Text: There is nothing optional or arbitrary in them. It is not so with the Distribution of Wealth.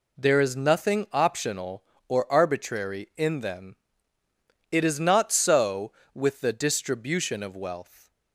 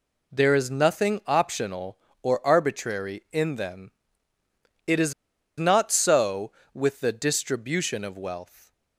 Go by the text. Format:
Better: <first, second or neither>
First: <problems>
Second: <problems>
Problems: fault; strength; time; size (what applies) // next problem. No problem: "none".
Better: first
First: none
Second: pauses between "is" and "not"; noticeable; at 5.1 s; 0.46 s long